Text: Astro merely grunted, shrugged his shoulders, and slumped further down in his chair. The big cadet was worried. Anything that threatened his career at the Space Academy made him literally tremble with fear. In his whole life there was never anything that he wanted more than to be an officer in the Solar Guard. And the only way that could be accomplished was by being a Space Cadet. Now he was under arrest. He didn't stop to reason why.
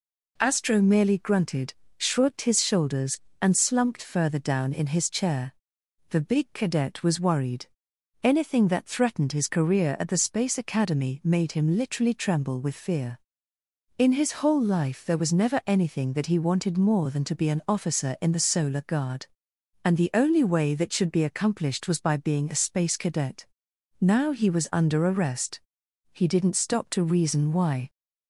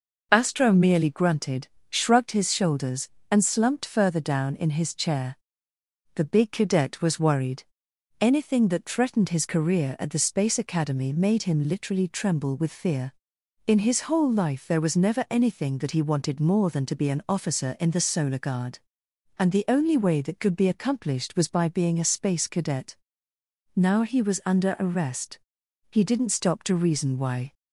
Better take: second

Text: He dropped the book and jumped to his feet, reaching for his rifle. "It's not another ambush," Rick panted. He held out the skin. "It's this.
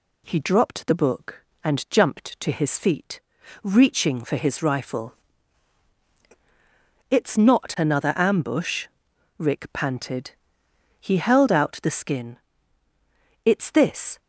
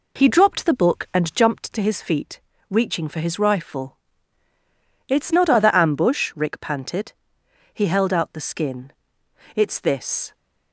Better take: first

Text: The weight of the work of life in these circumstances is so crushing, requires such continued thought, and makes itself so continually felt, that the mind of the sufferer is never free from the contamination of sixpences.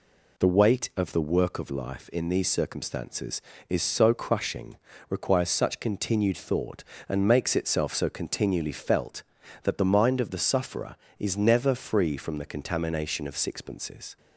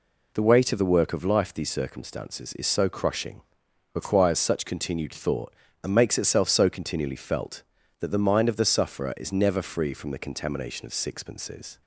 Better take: first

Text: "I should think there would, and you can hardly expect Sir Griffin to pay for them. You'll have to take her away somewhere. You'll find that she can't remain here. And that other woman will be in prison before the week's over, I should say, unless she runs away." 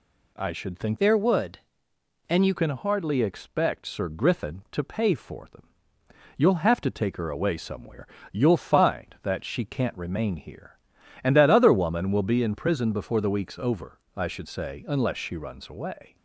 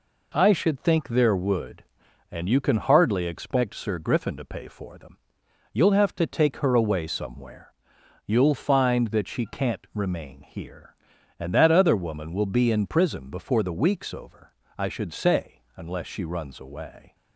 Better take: second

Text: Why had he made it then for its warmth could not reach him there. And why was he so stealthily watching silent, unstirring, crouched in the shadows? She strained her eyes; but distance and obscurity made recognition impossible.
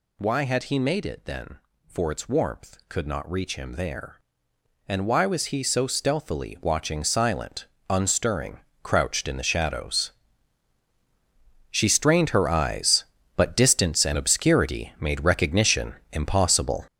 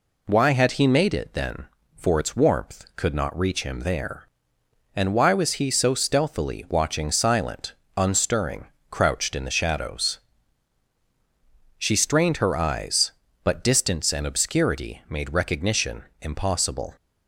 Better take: second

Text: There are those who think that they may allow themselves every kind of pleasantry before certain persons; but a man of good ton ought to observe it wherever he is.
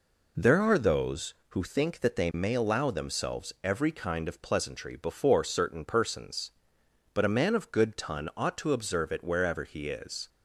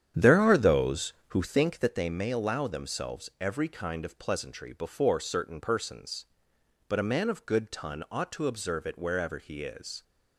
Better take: first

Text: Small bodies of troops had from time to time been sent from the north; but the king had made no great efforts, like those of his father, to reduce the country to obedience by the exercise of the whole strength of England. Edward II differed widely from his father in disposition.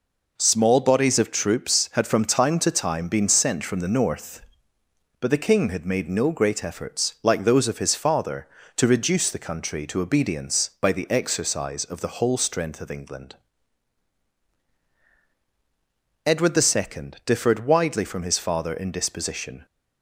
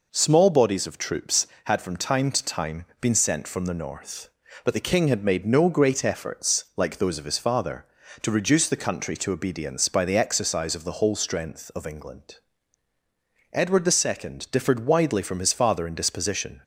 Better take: neither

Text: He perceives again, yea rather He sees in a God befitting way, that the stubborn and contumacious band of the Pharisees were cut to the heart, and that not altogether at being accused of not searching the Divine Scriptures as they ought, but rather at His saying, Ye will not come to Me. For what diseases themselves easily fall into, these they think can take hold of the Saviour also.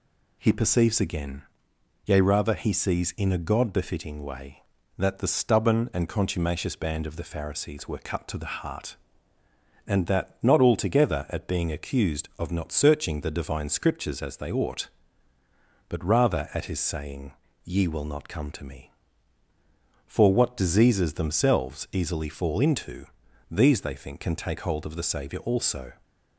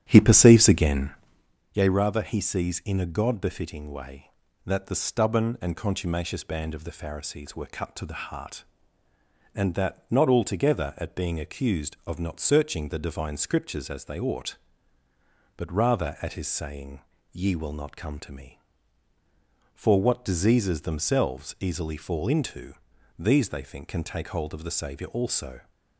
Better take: first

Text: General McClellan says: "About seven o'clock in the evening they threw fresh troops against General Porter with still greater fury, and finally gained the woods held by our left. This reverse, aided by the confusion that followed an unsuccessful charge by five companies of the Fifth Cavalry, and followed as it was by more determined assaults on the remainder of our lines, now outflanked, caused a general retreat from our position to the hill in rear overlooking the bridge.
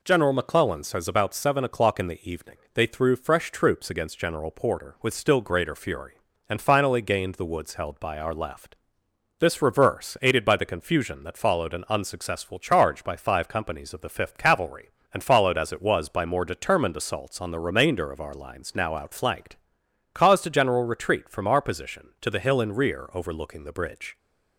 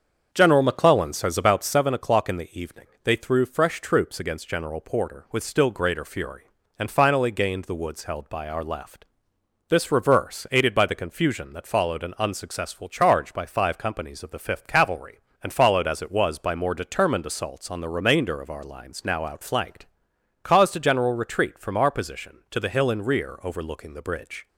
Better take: first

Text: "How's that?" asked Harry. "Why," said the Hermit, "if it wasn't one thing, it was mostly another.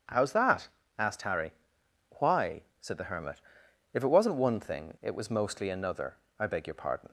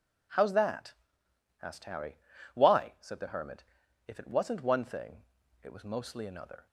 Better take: second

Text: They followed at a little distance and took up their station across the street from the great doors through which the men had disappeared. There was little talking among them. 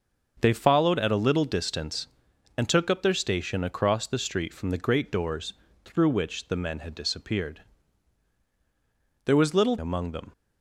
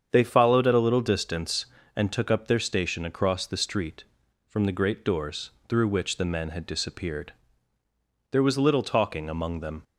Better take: second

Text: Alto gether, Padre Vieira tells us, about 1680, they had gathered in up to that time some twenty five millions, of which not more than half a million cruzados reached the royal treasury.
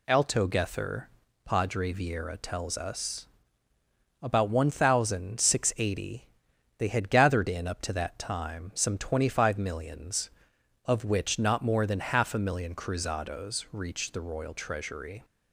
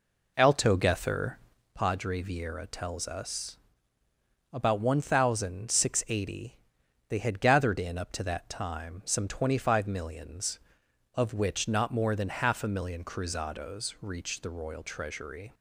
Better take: first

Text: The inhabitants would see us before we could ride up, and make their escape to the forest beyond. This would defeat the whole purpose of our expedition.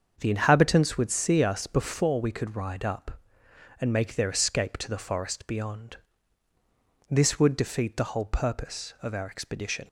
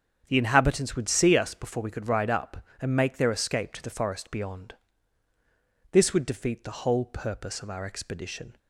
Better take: neither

